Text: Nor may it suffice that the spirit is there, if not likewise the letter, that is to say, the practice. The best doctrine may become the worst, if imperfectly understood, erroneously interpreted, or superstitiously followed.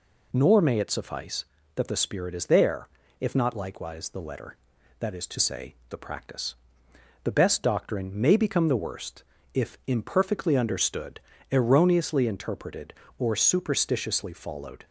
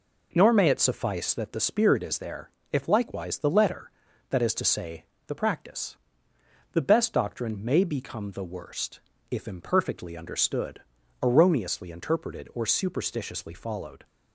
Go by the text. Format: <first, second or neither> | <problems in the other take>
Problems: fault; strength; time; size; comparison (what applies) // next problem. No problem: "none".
first | skips "not"; at 2.8 s